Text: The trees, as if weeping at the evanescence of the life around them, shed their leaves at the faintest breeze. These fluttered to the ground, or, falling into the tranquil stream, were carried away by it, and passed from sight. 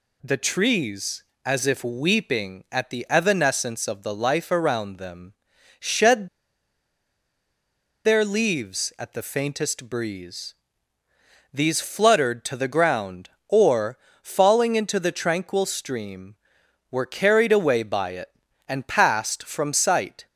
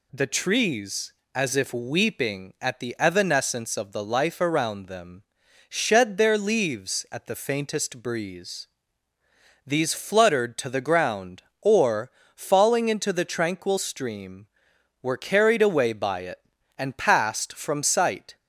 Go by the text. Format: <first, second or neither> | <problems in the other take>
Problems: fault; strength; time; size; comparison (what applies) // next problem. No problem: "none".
second | pauses between "shed" and "their"; strong; at 6.2 s; 1.7 s long